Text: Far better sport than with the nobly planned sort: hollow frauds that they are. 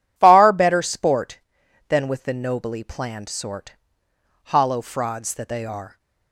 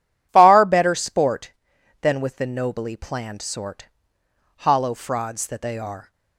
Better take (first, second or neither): neither